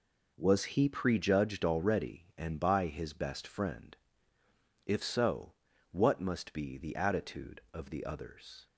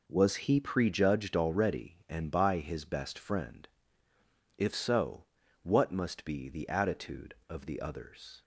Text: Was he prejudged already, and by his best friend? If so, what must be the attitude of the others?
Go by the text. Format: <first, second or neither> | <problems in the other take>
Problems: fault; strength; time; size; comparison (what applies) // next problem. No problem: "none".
neither | none